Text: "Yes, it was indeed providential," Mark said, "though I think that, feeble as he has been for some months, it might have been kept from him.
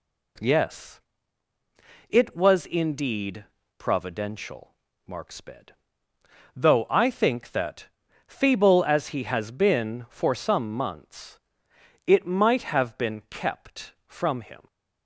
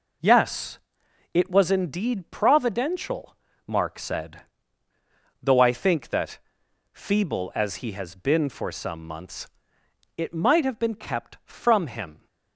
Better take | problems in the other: second | pauses between "indeed" and "providential"; slight; at 3.4 s; 0.32 s long // says "sped" for "said"; at 5.3 s

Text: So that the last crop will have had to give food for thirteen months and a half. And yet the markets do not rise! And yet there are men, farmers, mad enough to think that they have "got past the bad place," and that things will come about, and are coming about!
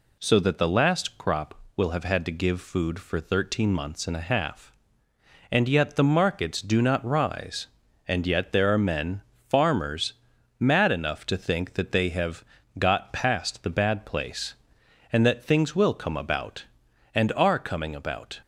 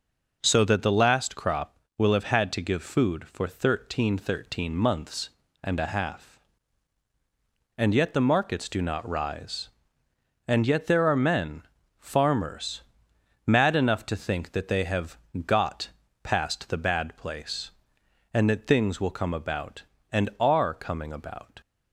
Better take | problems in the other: first | says "thirteen" twice; at 4.1 s // pauses between "have" and "got"; slight; at 15.1 s; 0.28 s long; slight in the first // pauses between "got" and "past"; slight; at 15.8 s; 0.34 s long

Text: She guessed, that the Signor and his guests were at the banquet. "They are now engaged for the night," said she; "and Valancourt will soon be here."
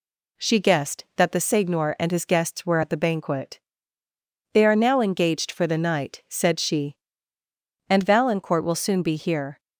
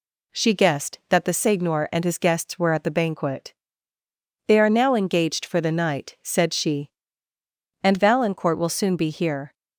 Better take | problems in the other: neither | none

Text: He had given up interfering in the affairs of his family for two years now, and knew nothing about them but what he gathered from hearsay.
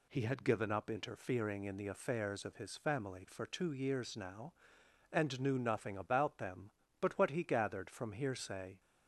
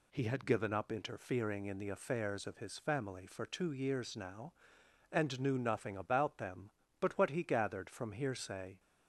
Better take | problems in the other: neither | none

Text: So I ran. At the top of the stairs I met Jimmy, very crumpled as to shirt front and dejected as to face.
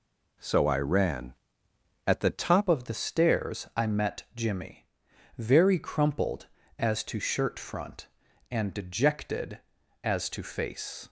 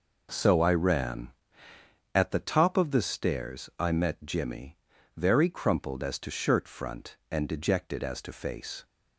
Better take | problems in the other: second | changes voice at "of"; from 2.6 s on; 8.4 s long

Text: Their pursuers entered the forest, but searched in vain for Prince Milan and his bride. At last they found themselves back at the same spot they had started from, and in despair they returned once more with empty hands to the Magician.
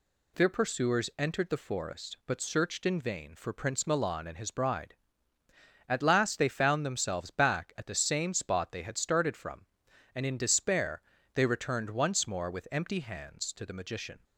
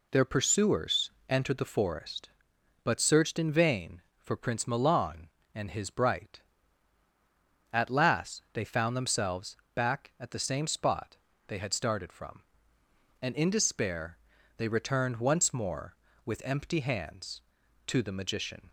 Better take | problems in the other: first | pauses between "pursuers" and "entered"; slight; at 1.1 s; 0.18 s long // says "bright" for "bride"; at 5.9 s // pauses between "themselves" and "back"; slight; at 9.5 s; 0.18 s long // pauses between "spot" and "they"; slight; at 11.1 s; 0.32 s long // pauses between "despair" and "they"; at 14.1 s; 0.40 s long; slight in the first

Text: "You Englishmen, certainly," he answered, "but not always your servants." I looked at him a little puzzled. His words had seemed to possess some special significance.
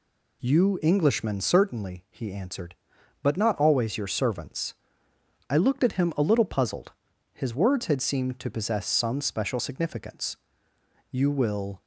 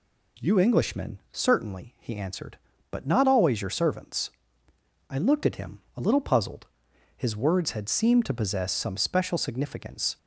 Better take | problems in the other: second | goes on to say "You will"; noticeable; from 11.1 s on; 0.70 s long

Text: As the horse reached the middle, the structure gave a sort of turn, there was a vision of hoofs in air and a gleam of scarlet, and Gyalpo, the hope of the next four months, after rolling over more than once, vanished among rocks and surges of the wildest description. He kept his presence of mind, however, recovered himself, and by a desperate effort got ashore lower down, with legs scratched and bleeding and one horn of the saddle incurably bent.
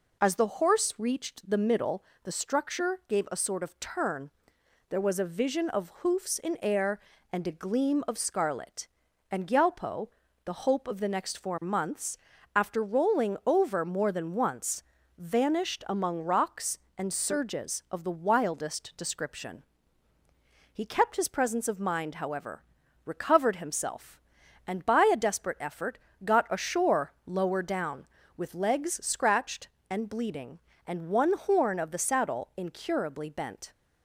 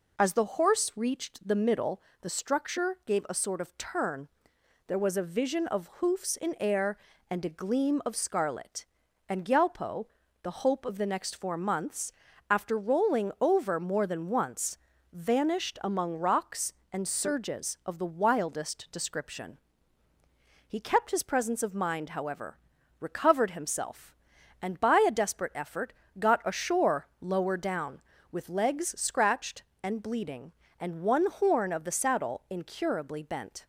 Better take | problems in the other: neither | pauses between "effort" and "got"; slight; the same in both // pauses between "ashore" and "lower"; slight; the same in both

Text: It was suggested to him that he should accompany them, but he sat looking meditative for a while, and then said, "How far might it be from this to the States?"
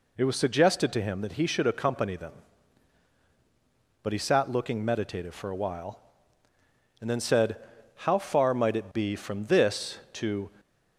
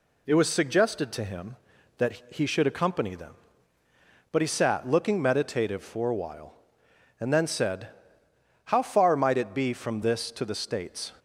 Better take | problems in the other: second | stops before "the States"; at 10.5 s

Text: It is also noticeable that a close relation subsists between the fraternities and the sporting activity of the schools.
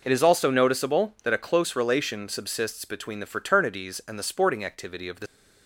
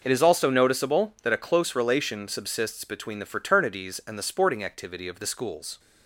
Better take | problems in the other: second | stops before "schools"; at 5.2 s

